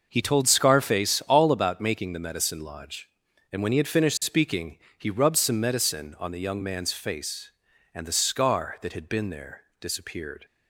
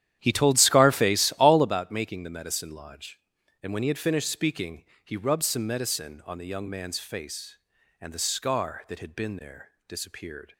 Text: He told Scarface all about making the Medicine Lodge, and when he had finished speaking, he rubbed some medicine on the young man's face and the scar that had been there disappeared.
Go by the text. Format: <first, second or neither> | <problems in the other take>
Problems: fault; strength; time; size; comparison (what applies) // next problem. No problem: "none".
first | starts louder than the rest; strong; until 1.8 s; 11 dB // pauses between "there" and "disappeared"; slight; at 9.7 s; 0.18 s long; slight in the first